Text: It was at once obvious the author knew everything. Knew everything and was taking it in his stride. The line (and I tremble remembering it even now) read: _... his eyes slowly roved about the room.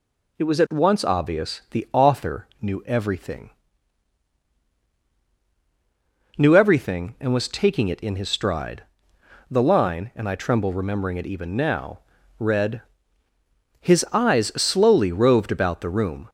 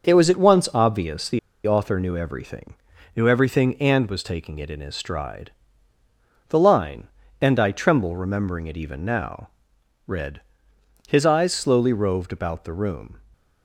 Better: first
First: none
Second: pauses between "the" and "author"; slight; at 1.3 s; 0.27 s long

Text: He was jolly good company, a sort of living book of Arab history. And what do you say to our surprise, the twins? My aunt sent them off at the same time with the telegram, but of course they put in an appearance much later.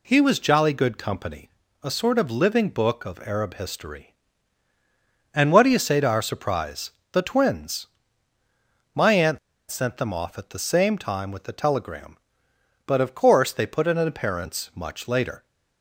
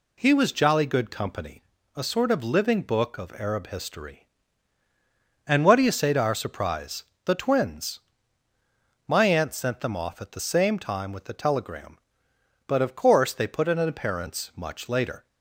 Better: second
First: pauses between "aunt" and "sent"; slight; at 9.3 s; 0.30 s long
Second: none

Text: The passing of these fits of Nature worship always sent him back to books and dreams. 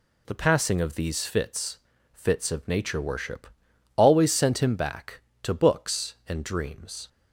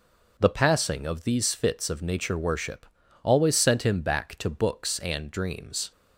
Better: second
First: says "fits" twice; at 2.1 s // pauses between "worship" and "always"; noticeable; at 3.4 s; 0.48 s long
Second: pauses between "worship" and "always"; at 2.8 s; 0.38 s long

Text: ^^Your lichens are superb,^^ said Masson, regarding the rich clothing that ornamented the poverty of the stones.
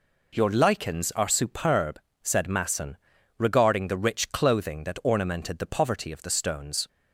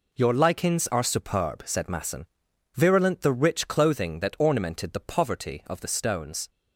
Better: first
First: none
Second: says "virulent" for "regarding"; at 2.7 s

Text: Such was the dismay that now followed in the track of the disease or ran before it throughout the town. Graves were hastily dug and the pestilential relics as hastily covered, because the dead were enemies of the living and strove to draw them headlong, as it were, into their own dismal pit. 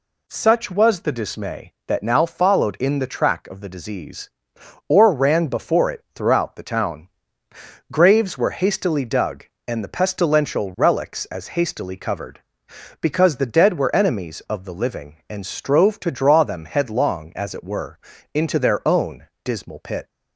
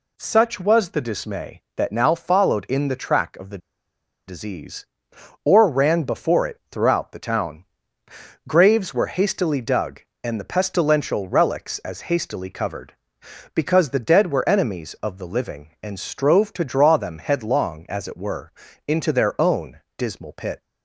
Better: first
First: pauses between "own" and "dismal"; slight; at 19.2 s; 0.18 s long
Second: pauses between "the" and "disease"; noticeable; at 3.5 s; 0.69 s long // pauses between "own" and "dismal"; slight; at 19.7 s; 0.18 s long

